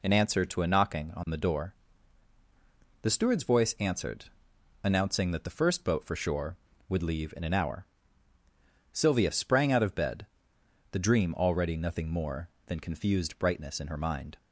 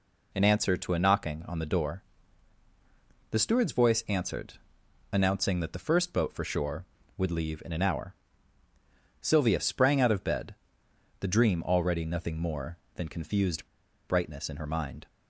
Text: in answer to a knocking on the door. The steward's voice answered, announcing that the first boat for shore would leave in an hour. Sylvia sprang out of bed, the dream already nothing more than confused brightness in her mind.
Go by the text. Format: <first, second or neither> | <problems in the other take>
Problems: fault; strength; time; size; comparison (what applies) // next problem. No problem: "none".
first | pauses between "confused" and "brightness"; at 13.6 s; 0.40 s long